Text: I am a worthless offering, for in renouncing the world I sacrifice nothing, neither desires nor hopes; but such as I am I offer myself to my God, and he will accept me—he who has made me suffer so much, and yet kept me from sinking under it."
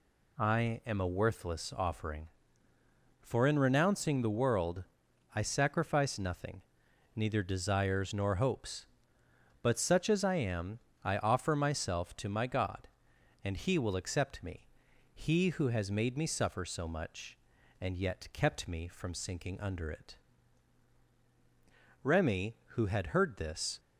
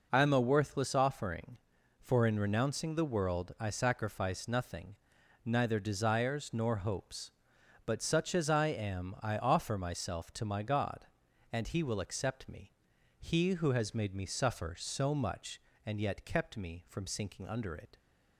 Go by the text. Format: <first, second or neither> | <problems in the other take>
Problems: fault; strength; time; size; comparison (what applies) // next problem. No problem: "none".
second | pauses between "world" and "I"; noticeable; at 4.8 s; 0.50 s long // pauses between "am" and "I"; slight; at 10.7 s; 0.26 s long // goes on to say "Remy who had heard this"; strong; from 22.0 s on; 1.7 s long